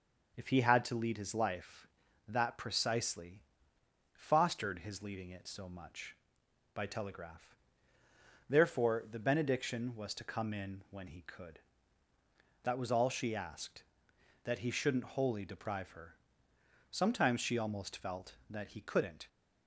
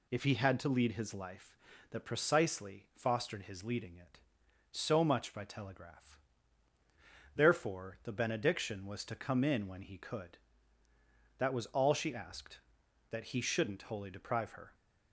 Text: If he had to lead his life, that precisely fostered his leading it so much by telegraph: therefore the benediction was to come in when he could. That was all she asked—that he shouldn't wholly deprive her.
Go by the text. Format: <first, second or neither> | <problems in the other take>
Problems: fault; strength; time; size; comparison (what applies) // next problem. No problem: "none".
second | pauses between "precisely" and "fostered"; noticeable; at 3.4 s; 0.72 s long // goes on to say "Sometimes she almost felt that he couldn't"; strong; from 16.8 s on; 2.3 s long